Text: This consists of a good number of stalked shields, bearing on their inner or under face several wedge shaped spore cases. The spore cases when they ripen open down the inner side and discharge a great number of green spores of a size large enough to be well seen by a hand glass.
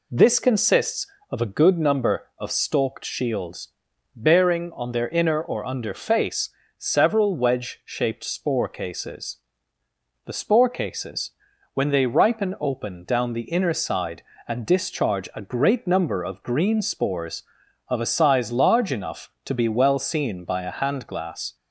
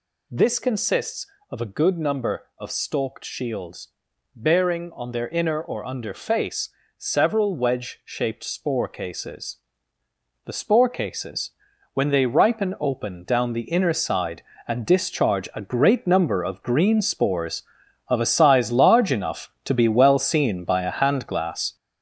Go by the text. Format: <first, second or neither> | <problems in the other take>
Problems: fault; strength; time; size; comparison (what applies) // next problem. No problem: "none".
first | gets louder; strong; throughout; 7 dB // pauses between "face" and "several"; slight; at 6.6 s; 0.28 s long; slight in the first // pauses between "cases" and "when"; at 11.5 s; 0.42 s long; also in the first